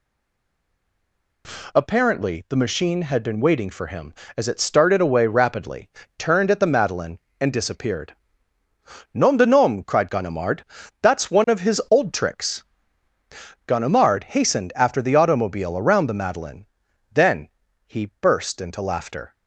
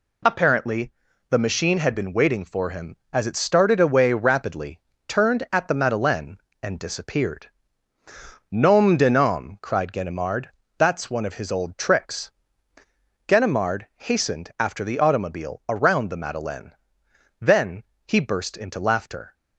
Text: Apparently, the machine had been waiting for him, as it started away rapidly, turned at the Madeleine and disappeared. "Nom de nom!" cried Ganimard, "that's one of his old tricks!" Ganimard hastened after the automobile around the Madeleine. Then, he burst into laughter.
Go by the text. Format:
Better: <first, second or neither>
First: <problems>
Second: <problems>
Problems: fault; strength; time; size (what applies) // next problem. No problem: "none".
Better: second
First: stays silent before the first word; noticeable; until 1.4 s; 1.4 s long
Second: none